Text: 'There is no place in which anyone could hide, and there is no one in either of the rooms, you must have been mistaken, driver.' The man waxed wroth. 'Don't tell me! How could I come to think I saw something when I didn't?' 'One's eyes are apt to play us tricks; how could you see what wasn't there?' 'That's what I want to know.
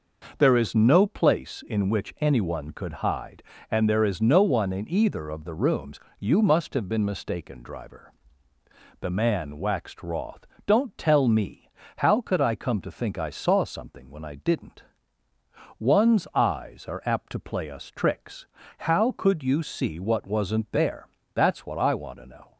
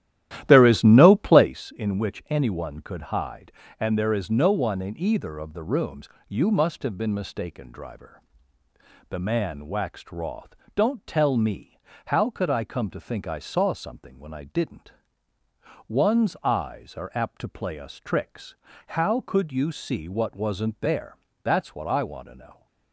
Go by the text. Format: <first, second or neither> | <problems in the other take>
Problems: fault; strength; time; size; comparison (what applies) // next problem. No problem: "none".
first | starts louder than the rest; strong; until 1.6 s; 13 dB